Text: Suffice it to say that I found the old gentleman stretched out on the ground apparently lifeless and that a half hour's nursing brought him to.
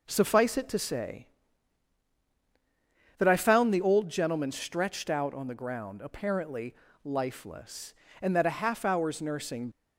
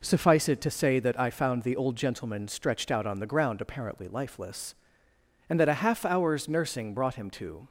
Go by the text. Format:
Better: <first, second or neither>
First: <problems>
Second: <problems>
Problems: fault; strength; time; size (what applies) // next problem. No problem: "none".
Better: second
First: pauses between "apparently" and "lifeless"; slight; at 6.7 s; 0.30 s long // stops before "brought him to"; at 9.7 s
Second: none